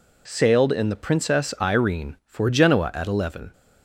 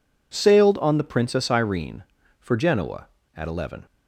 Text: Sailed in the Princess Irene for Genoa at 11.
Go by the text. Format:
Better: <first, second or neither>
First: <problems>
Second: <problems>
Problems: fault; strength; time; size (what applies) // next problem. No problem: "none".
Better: first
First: none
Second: says "on" for "in"; at 0.7 s